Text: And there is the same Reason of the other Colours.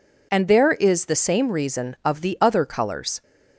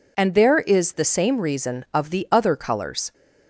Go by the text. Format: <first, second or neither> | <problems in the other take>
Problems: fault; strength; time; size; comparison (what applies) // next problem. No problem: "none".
neither | none